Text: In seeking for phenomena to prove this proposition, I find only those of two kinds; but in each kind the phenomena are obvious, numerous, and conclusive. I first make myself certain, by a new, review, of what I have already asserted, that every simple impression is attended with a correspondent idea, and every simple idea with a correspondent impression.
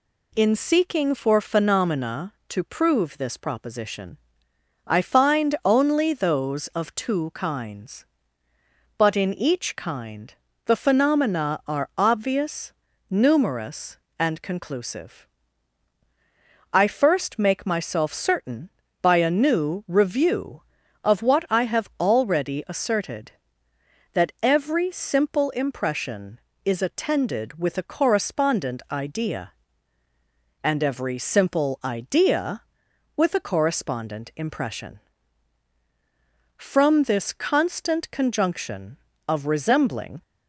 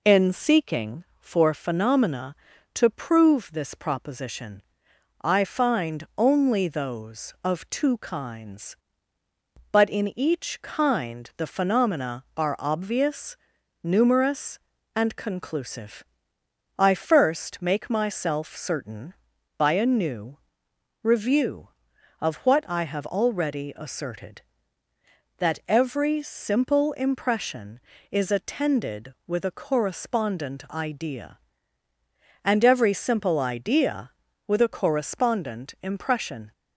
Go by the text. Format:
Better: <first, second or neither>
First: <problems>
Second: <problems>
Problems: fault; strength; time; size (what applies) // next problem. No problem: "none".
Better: second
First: pauses between "kind" and "the"; slight; at 10.3 s; 0.32 s long // goes on to say "From this constant conjunction of resembling"; strong; from 36.5 s on; 3.6 s long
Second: none